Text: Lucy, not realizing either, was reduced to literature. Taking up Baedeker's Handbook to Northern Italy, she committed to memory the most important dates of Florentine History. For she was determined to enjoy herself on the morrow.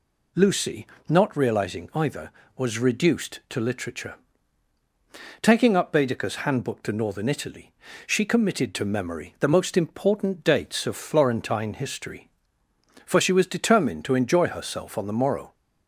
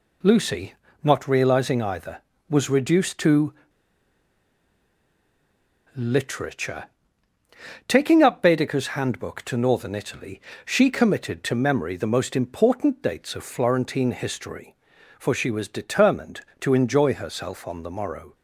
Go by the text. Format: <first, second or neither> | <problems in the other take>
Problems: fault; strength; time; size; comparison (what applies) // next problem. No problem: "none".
first | pauses between "to" and "literature"; strong; at 3.5 s; 2.4 s long